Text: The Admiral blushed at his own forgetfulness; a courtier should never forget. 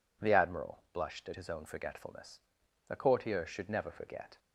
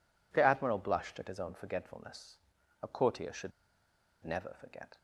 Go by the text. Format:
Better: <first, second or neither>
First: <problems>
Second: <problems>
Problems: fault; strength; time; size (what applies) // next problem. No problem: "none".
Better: first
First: none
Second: pauses between "should" and "never"; noticeable; at 3.5 s; 0.72 s long